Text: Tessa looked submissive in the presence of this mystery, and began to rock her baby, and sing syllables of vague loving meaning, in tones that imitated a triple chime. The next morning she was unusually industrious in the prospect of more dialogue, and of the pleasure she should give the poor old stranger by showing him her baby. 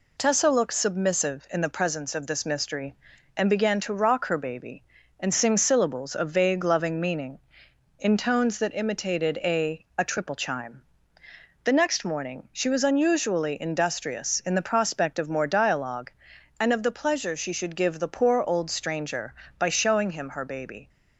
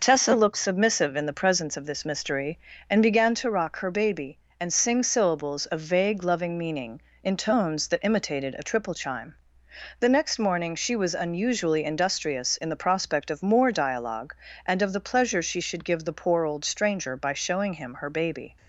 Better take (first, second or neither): second